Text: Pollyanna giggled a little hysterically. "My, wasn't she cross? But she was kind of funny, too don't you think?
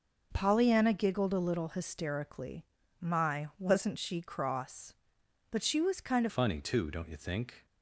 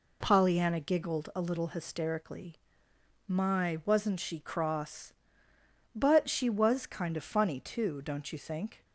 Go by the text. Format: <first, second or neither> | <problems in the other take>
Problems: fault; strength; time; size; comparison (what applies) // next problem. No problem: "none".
second | changes voice at "funny"; from 6.2 s on; 1.4 s long